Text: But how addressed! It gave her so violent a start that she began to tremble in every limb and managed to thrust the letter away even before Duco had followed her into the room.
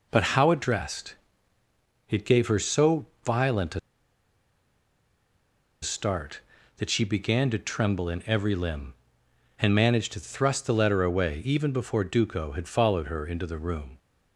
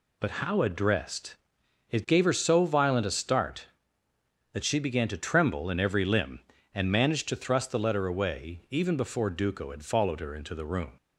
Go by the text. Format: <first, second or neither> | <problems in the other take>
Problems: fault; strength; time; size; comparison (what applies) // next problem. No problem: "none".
second | pauses between "so" and "violent"; slight; at 3.0 s; 0.18 s long // pauses between "a" and "start"; strong; at 3.7 s; 2.0 s long